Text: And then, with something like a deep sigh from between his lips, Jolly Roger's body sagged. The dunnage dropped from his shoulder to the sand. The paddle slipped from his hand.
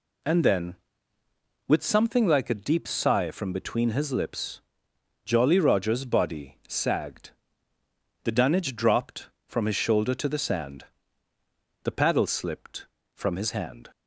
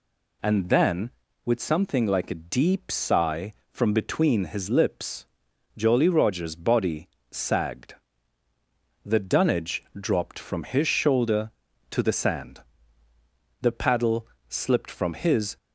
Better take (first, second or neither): first